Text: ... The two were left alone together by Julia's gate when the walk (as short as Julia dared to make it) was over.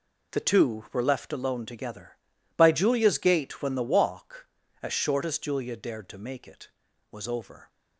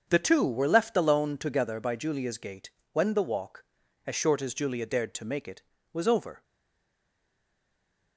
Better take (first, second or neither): first